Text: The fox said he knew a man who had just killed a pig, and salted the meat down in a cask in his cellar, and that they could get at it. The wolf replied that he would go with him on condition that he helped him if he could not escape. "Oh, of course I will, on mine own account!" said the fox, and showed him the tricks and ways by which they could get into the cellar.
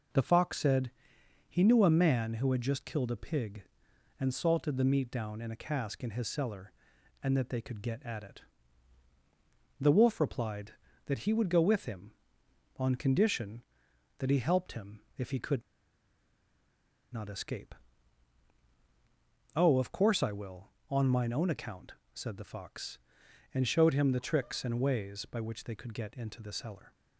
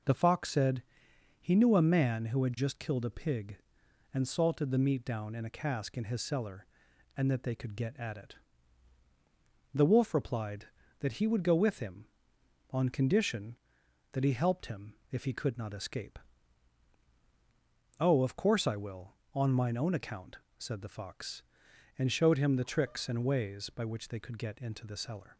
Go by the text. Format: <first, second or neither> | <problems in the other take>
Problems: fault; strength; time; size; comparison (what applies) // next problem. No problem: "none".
second | pauses between "said" and "he"; noticeable; at 0.9 s; 0.58 s long; noticeable in the second // pauses between "him" and "if"; slight; at 14.9 s; 0.18 s long; slight in the second // pauses between "could" and "not"; strong; at 15.6 s; 1.5 s long